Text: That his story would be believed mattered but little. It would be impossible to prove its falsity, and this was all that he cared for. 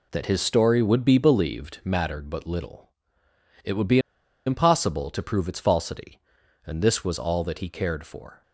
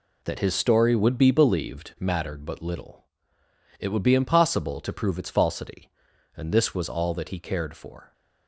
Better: second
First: pauses between "be" and "impossible"; noticeable; at 3.9 s; 0.47 s long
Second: none

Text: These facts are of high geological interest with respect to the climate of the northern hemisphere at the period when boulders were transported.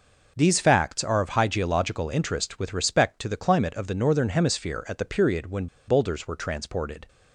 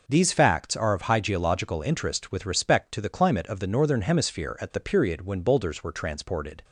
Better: second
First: pauses between "when" and "boulders"; slight; at 5.6 s; 0.20 s long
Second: none

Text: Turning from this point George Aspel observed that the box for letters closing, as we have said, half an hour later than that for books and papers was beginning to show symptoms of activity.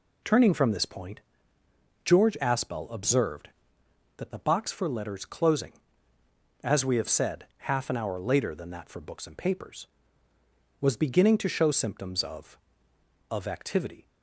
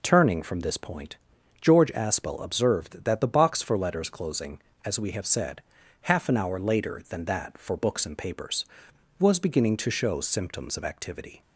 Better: second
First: pauses between "point" and "George"; noticeable; at 1.2 s; 0.84 s long // says "of" twice; at 13.2 s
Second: pauses between "point" and "George"; at 1.1 s; 0.44 s long

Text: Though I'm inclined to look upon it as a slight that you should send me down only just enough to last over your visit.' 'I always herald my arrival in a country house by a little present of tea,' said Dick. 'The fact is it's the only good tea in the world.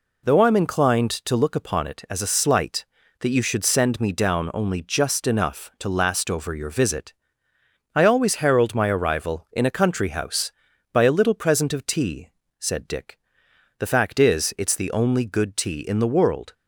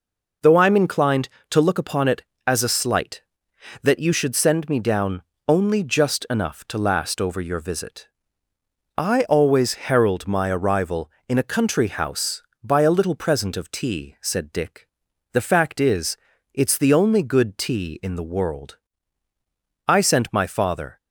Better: first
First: none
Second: pauses between "down" and "only"; slight; at 5.2 s; 0.24 s long // pauses between "is" and "it's"; at 16.1 s; 0.38 s long // goes on to say "I sent my father"; noticeable; from 19.8 s on; 1.1 s long

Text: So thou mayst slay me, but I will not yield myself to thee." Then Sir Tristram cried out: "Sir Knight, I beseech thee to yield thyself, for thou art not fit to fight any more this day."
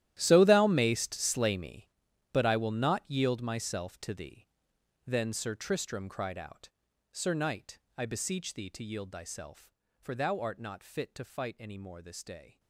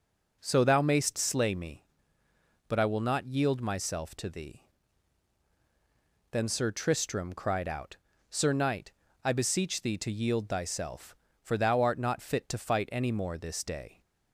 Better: second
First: gets quieter; strong; throughout; 17.5 dB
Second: none

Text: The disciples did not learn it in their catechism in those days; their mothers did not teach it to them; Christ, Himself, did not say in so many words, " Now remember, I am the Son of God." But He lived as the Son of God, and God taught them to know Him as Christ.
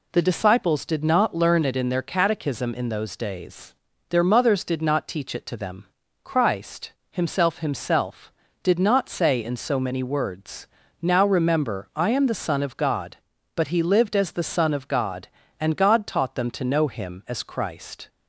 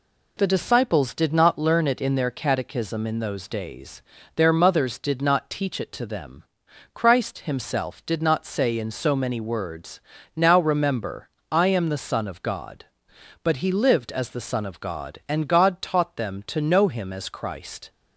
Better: second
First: says "Himself" twice; at 7.5 s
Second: none

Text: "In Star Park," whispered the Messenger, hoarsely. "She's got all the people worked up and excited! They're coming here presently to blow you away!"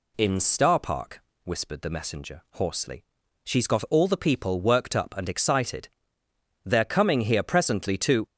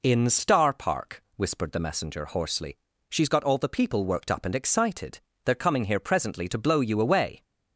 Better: second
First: stops before "blow you away"; at 8.2 s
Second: none

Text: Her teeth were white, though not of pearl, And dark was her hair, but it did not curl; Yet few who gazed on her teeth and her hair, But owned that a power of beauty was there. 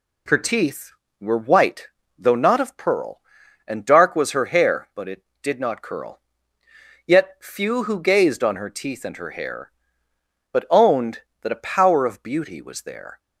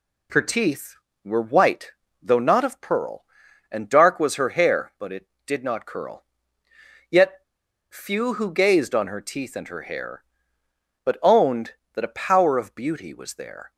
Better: first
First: none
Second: pauses between "Yet" and "few"; noticeable; at 7.4 s; 0.46 s long

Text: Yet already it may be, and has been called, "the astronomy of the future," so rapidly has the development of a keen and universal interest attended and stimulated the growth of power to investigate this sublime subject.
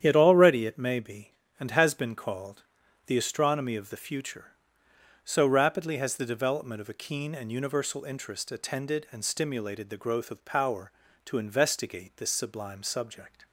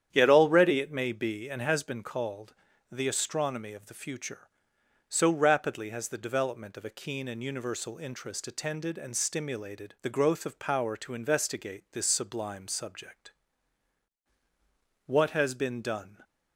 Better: first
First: starts louder than the rest; strong; until 1.0 s; 9.5 dB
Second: starts louder than the rest; strong; until 1.1 s; 9.5 dB // goes on to say "What has been done"; noticeable; from 15.0 s on; 1.1 s long

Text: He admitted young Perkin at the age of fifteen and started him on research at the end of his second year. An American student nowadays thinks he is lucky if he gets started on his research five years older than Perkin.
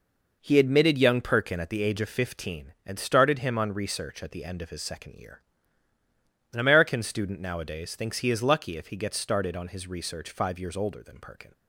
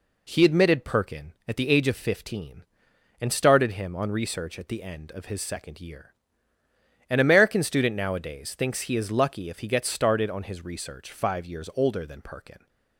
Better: first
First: none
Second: skips "young"; at 0.8 s

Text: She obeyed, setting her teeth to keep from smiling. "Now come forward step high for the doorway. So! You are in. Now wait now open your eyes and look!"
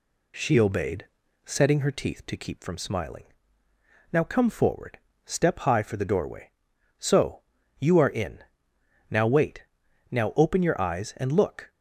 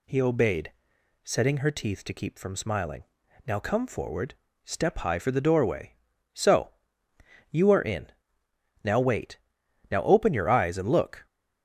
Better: first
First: pauses between "forward" and "step"; slight; at 4.9 s; 0.26 s long // pauses between "wait" and "now"; noticeable; at 9.6 s; 0.48 s long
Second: says "He" for "She"; at 0.0 s // pauses between "forward" and "step"; slight; at 4.3 s; 0.30 s long // pauses between "wait" and "now"; noticeable; at 9.3 s; 0.52 s long

